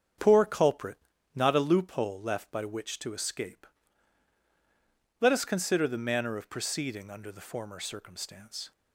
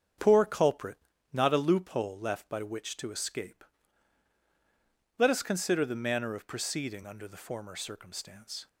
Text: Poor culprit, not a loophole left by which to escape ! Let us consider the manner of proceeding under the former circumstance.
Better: neither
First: starts louder than the rest; strong; until 1.5 s; 7.5 dB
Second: starts louder than the rest; strong; until 1.5 s; 7.5 dB

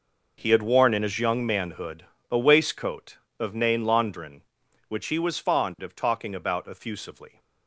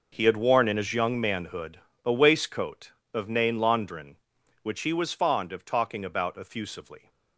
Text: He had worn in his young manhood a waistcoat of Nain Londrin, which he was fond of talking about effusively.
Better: neither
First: pauses between "manhood" and "a"; slight; at 2.0 s; 0.26 s long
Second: pauses between "manhood" and "a"; slight; at 1.7 s; 0.26 s long

